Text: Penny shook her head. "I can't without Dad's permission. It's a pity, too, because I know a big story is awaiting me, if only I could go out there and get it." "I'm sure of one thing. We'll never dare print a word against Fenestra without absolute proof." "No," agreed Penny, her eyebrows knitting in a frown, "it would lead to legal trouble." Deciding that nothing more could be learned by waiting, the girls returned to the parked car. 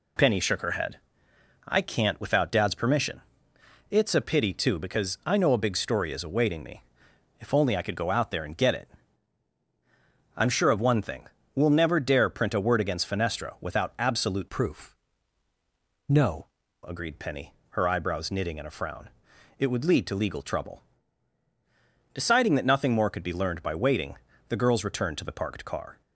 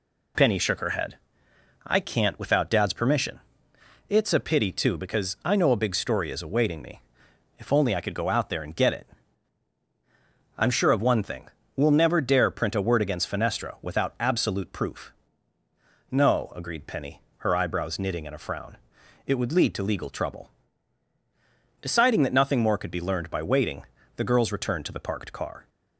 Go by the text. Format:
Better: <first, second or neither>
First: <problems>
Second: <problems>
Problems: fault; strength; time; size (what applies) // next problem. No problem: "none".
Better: second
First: changes voice from "proof" to "No"; from 14.4 to 16.4 s; 2.0 s long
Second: none